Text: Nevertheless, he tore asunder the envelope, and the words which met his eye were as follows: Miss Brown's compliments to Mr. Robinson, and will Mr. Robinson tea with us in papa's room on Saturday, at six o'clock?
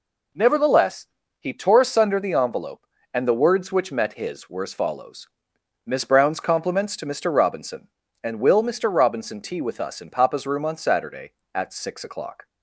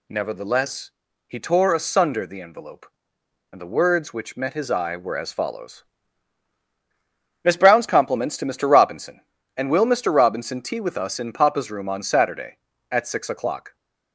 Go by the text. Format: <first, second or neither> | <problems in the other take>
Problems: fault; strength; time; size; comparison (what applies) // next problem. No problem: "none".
second | skips "eye"; at 4.4 s